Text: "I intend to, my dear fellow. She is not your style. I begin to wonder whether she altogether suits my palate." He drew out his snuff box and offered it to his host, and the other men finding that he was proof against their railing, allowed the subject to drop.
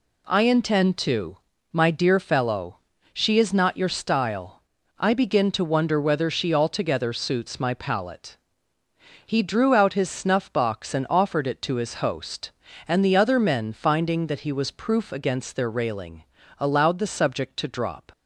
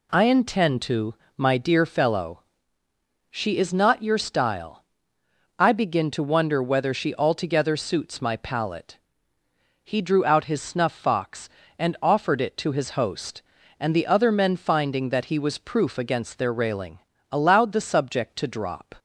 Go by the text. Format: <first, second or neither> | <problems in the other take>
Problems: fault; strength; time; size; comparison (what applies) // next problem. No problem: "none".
first | says "fox" for "box"; at 10.9 s